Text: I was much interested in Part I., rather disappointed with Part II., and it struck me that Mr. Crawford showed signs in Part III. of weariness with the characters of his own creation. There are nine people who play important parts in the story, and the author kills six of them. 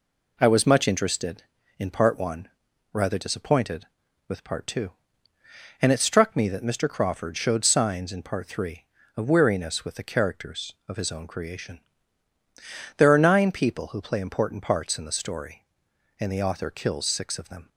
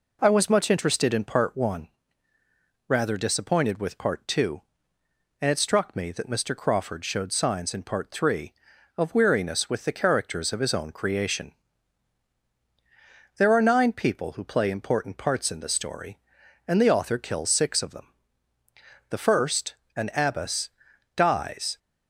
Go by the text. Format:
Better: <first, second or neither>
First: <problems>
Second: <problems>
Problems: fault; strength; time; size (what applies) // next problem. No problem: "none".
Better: first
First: none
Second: goes on to say "The first an abbess dies"; strong; from 19.0 s on; 2.7 s long